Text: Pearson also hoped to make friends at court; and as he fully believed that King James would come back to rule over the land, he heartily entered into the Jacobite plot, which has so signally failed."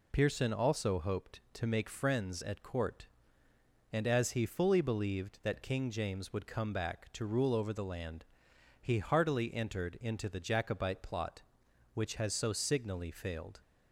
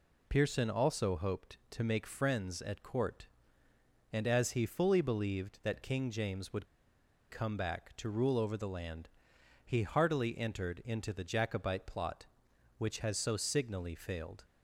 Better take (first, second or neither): first